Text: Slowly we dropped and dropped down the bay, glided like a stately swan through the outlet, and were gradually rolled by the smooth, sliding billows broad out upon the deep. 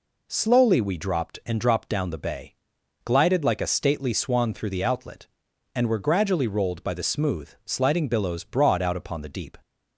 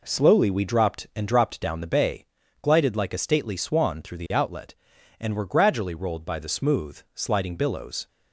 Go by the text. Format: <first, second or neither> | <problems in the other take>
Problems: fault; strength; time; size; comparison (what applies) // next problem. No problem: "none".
first | stops before "broad out upon the deep"; at 8.0 s